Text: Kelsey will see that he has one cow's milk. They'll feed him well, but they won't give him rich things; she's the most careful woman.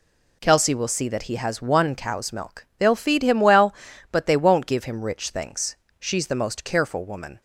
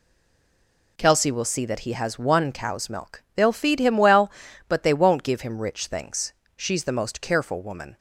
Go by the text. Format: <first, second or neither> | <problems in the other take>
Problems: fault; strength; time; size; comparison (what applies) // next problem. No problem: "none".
first | stays silent before the first word; until 0.9 s; 0.9 s long